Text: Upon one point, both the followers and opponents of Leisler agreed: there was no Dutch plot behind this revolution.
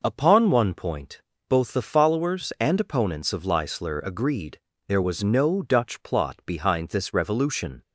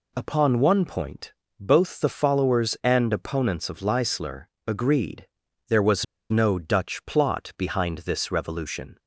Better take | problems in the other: first | pauses between "Leisler" and "agreed"; slight; at 4.4 s; 0.20 s long // pauses between "was" and "no"; slight; at 6.0 s; 0.25 s long

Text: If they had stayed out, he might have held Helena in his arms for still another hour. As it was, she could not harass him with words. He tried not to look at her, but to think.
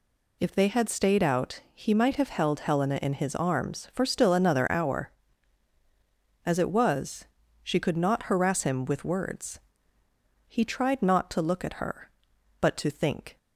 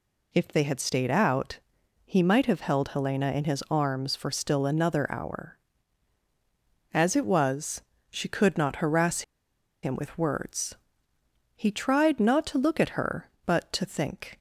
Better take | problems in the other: first | pauses between "harass" and "him"; noticeable; at 9.2 s; 0.61 s long

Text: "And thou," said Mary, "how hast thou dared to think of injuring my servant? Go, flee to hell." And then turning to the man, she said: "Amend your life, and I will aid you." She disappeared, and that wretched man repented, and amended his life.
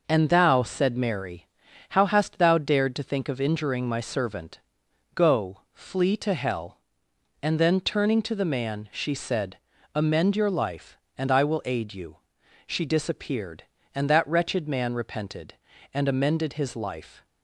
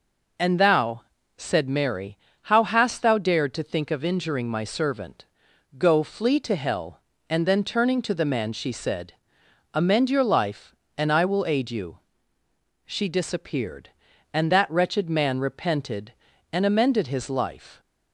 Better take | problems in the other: neither | none

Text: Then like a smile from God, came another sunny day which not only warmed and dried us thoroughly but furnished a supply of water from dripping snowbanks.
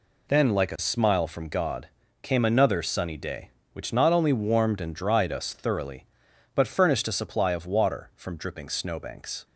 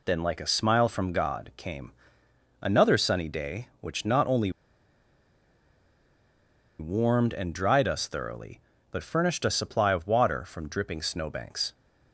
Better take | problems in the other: first | pauses between "came" and "another"; noticeable; at 1.9 s; 0.68 s long // pauses between "only" and "warmed"; strong; at 4.5 s; 2.2 s long

